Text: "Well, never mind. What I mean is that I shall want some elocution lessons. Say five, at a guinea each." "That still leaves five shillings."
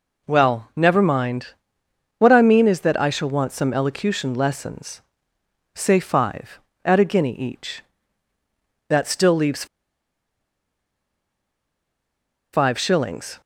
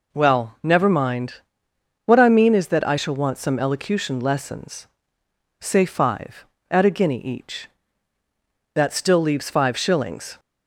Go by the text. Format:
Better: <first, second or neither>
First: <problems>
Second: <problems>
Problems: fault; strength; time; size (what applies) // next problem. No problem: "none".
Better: second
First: pauses between "leaves" and "five"; strong; at 9.6 s; 2.8 s long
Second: none